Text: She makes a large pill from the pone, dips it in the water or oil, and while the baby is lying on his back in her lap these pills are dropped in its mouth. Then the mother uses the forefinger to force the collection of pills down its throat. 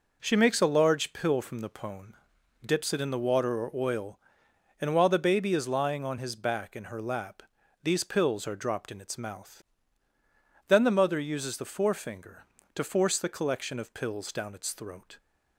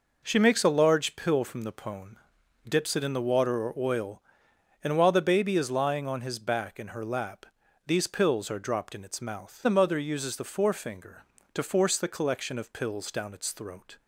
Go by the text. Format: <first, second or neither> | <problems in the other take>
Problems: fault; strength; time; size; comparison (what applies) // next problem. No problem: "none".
first | pauses between "lap" and "these"; at 7.4 s; 0.42 s long; also in the first // skips "Then"; at 9.6 s